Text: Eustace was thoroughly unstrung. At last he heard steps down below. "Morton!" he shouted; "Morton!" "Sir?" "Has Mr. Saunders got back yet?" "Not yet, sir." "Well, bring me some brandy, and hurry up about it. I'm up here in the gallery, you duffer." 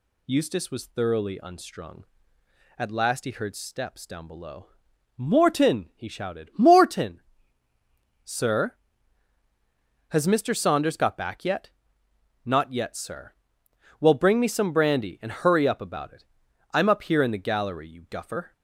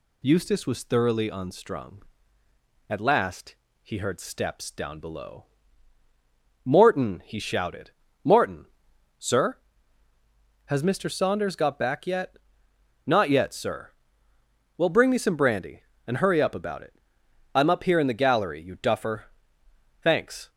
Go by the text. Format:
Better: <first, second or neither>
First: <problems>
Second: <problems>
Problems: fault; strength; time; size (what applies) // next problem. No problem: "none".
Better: first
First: none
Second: pauses between "last" and "he"; slight; at 3.5 s; 0.28 s long // goes on to say "Thanks"; slight; from 20.0 s on; 0.46 s long